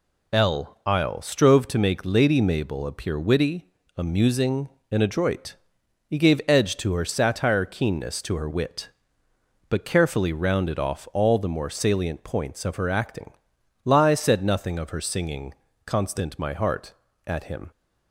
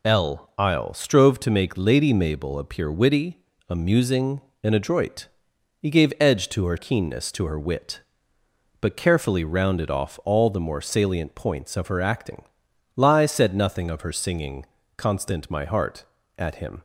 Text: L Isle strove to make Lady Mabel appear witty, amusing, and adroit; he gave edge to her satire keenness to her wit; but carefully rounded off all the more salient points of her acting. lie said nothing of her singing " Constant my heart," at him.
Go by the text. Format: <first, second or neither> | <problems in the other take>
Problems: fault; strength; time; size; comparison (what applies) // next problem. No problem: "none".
first | skips "satire"; at 6.7 s